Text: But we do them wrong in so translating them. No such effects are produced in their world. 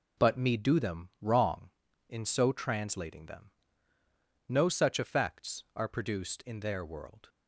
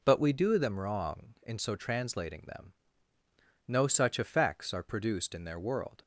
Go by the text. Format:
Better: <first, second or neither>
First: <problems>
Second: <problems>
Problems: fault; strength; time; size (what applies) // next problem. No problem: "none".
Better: second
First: says "me" for "we"; at 0.3 s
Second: none